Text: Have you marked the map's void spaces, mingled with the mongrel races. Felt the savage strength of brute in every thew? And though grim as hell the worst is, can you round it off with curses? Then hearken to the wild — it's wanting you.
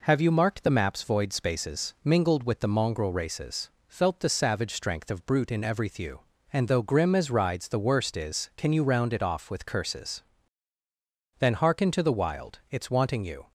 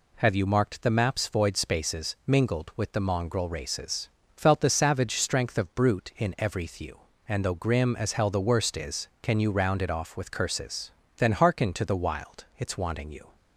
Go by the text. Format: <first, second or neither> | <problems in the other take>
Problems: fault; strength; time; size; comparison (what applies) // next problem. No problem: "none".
second | says "rides" for "hell"; at 7.2 s